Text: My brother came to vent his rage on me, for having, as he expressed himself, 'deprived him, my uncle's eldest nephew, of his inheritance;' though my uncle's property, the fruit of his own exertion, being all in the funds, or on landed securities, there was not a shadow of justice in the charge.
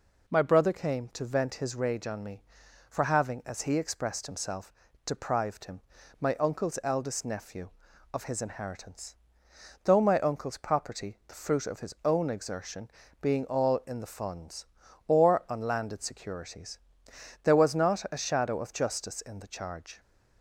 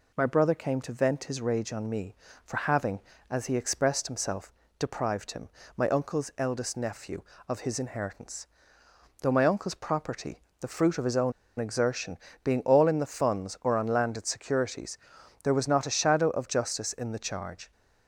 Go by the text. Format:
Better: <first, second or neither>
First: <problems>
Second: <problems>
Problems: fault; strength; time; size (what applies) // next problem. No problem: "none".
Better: first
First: none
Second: pauses between "own" and "exertion"; slight; at 11.3 s; 0.26 s long